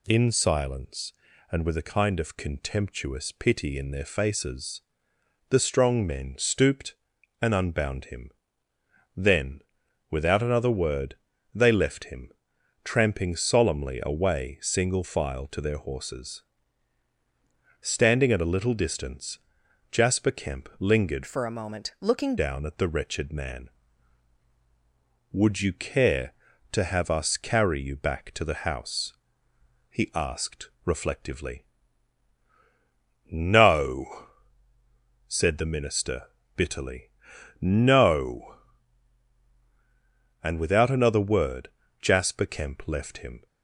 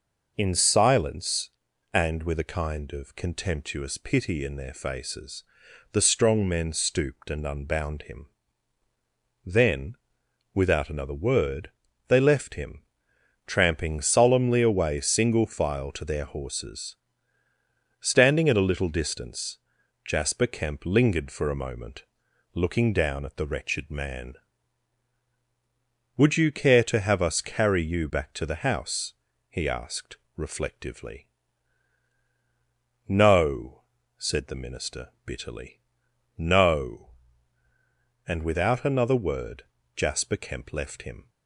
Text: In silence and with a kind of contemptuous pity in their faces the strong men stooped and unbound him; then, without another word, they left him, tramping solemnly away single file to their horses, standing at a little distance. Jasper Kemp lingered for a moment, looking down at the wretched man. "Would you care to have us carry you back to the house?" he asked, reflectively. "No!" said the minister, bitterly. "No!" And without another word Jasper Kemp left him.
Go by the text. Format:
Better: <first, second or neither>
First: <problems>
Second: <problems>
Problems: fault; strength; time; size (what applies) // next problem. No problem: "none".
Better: second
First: pauses between "faces" and "the"; noticeable; at 4.8 s; 0.68 s long // changes voice from "for" to "looking"; from 21.2 to 22.3 s; 1.1 s long // pauses between "word" and "Jasper"; slight; at 41.6 s; 0.30 s long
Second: pauses between "faces" and "the"; noticeable; at 5.4 s; 0.48 s long // pauses between "word" and "Jasper"; slight; at 39.6 s; 0.32 s long